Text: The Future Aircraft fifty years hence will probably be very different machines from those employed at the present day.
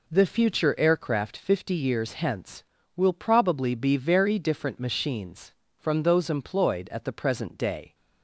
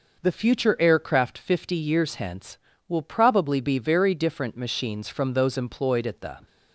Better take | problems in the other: first | stops before "present day"; at 6.4 s

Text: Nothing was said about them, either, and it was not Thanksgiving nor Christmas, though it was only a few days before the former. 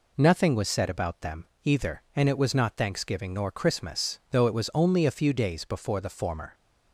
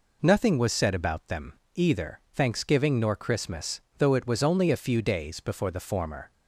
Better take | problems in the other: first | skips "and it was not"; at 2.2 s

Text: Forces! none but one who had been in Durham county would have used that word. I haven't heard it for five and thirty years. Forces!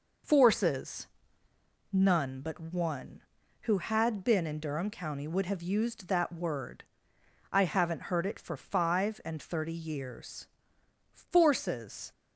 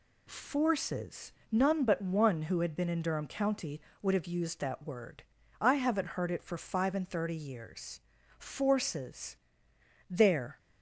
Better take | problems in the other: first | goes on to say "there"; slight; from 10.0 s on; 0.48 s long

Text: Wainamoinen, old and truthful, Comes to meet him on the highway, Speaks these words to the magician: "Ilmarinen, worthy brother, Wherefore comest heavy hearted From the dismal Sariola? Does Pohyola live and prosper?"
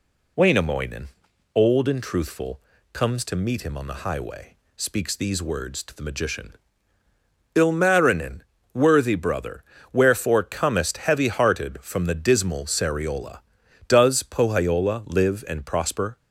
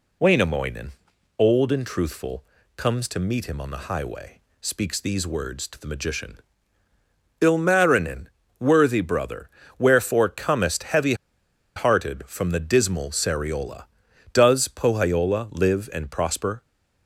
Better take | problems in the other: first | pauses between "heavy" and "hearted"; noticeable; at 11.1 s; 0.61 s long

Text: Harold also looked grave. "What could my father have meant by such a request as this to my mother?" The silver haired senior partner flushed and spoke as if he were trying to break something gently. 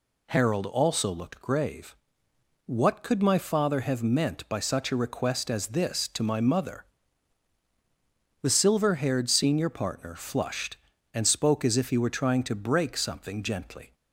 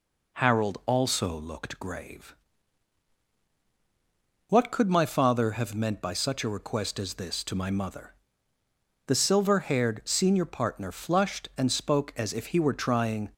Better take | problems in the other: first | stops before "to break something gently"; at 13.3 s

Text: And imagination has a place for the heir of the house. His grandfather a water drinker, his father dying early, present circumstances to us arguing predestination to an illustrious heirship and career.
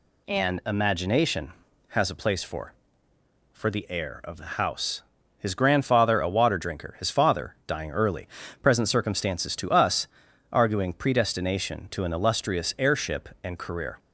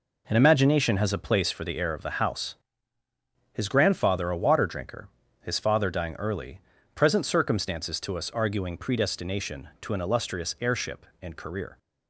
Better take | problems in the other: second | says "for" twice; at 3.5 s // pauses between "us" and "arguing"; at 10.0 s; 0.44 s long

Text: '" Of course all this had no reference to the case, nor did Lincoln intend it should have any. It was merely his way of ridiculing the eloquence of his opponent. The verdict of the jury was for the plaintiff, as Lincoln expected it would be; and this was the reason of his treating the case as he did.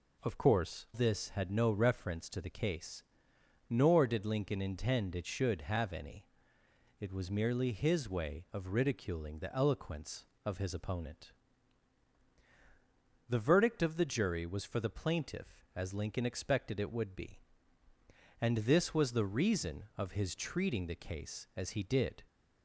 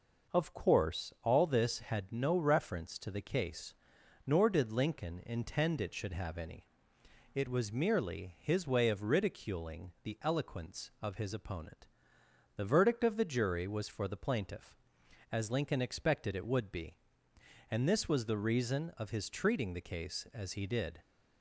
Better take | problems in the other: second | skips "all"; at 0.8 s

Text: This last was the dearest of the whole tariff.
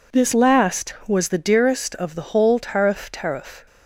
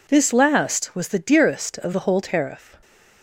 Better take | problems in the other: second | says "tariff" twice; at 3.0 s

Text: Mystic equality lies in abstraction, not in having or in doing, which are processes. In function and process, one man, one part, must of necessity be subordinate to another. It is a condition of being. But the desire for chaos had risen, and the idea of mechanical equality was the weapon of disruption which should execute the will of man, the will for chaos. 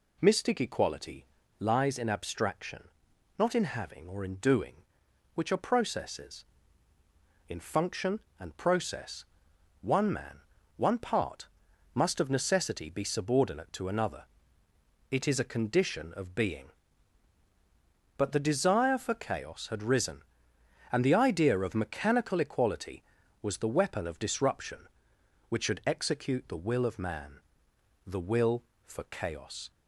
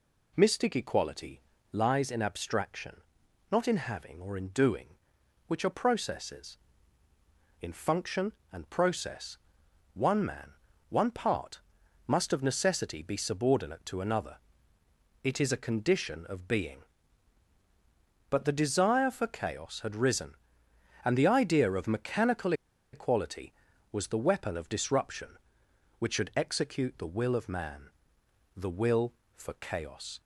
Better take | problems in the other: first | pauses between "equality" and "lies"; slight; at 1.4 s; 0.30 s long; slight in the first // pauses between "mechanical" and "equality"; at 22.5 s; 0.40 s long

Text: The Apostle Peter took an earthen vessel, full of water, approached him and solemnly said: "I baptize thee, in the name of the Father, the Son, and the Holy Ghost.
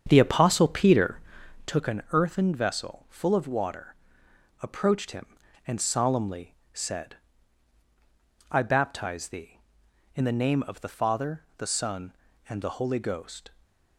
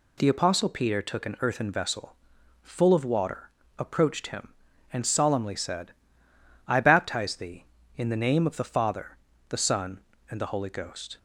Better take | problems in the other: second | starts louder than the rest; strong; until 1.8 s; 8 dB // pauses between "Peter" and "took"; noticeable; at 1.1 s; 0.46 s long // pauses between "solemnly" and "said"; slight; at 6.5 s; 0.16 s long // stays silent after the last word; slight; from 13.4 s on; 0.5 s long

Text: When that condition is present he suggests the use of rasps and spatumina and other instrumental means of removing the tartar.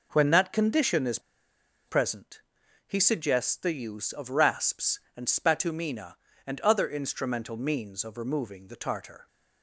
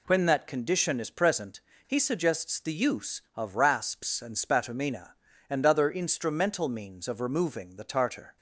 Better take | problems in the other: second | pauses between "is" and "present"; noticeable; at 1.1 s; 0.67 s long // pauses between "present" and "he"; noticeable; at 2.4 s; 0.46 s long; slight in the second

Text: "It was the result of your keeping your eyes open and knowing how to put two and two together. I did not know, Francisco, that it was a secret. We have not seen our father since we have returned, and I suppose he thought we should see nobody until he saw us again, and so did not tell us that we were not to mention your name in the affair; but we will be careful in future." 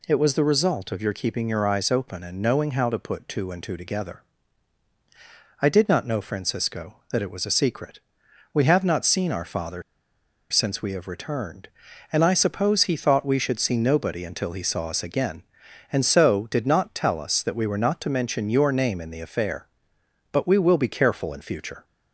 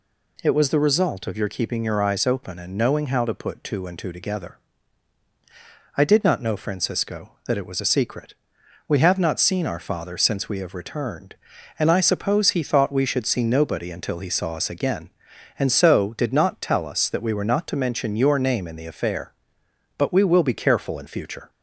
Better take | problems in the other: second | pauses between "father" and "since"; noticeable; at 9.8 s; 0.68 s long

